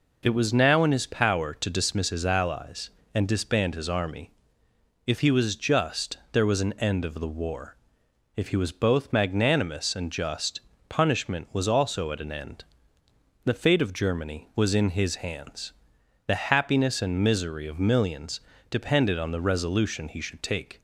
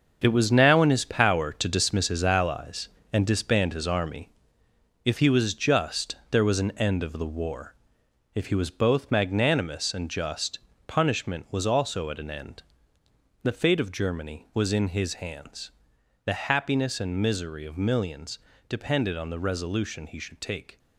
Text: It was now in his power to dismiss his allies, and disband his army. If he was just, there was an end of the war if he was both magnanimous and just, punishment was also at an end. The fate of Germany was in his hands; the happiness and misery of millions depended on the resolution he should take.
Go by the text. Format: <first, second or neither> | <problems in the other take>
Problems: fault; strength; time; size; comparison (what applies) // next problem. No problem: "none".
first | gets quieter; strong; throughout; 9.5 dB // pauses between "war" and "if"; noticeable; at 7.7 s; 0.60 s long; noticeable in the first // pauses between "millions" and "depended"; slight; at 18.3 s; 0.30 s long; slight in the first